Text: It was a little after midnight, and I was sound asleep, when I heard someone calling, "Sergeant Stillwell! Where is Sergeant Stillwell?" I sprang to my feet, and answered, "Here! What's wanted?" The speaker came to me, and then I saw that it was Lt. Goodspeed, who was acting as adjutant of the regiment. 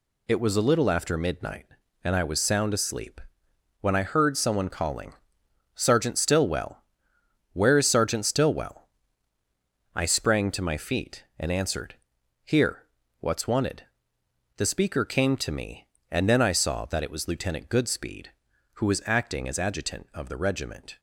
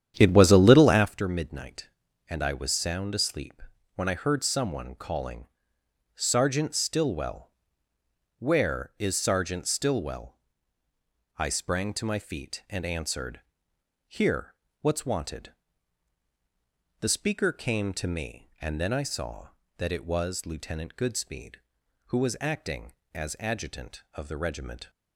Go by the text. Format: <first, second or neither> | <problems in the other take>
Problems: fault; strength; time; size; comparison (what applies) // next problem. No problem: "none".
first | starts louder than the rest; strong; until 1.1 s; 9.5 dB